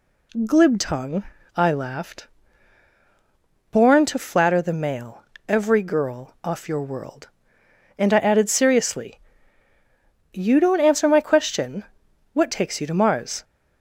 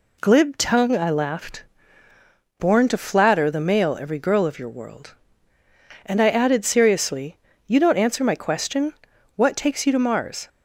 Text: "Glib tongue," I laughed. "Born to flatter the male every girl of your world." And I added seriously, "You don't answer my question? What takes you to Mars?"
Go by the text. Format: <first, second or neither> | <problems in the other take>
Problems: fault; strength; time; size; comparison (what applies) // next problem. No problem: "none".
second | pauses between "male" and "every"; slight; at 5.2 s; 0.24 s long // says "off" for "of"; at 6.4 s